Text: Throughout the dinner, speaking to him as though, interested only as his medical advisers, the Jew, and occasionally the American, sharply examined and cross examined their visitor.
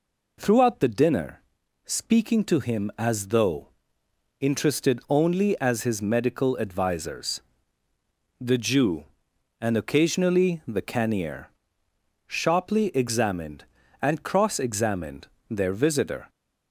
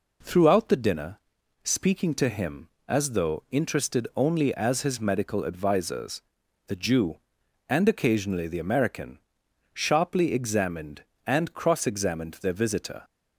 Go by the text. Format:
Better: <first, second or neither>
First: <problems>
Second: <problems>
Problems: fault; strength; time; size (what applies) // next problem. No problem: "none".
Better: second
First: says "Cannier" for "American"; at 10.8 s // pauses between "examined" and "their"; slight; at 15.2 s; 0.22 s long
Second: none